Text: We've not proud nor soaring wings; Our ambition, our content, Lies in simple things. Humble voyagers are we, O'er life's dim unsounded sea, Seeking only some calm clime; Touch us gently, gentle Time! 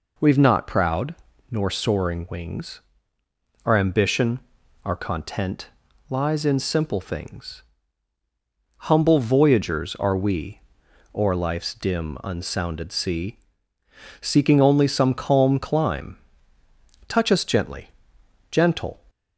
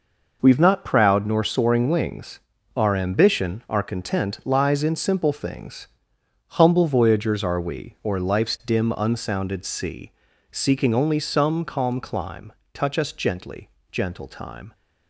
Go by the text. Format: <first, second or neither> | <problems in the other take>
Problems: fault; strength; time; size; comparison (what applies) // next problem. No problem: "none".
second | pauses between "proud" and "nor"; slight; at 1.1 s; 0.36 s long // stops before "Time"; at 19.0 s